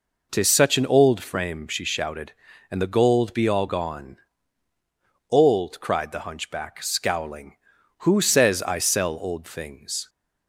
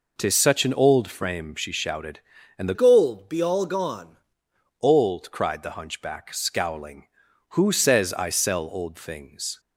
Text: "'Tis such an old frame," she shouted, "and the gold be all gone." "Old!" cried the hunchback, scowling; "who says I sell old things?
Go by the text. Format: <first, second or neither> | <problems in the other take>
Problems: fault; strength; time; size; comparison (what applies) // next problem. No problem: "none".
first | changes voice from "gold" to "gone"; from 2.7 to 4.1 s; 1.4 s long